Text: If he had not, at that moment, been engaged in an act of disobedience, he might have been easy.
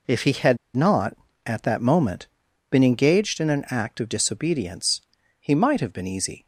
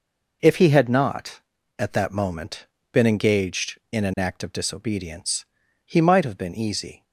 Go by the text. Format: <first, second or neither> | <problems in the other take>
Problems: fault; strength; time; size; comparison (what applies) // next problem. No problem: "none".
second | pauses between "had" and "not"; slight; at 0.5 s; 0.18 s long